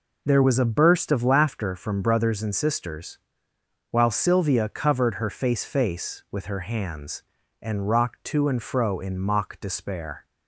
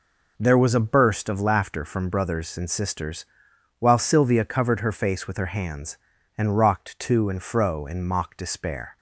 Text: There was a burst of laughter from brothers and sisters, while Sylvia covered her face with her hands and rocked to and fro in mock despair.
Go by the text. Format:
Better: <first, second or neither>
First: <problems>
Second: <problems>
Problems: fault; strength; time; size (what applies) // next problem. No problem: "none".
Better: second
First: says "face" twice; at 5.6 s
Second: none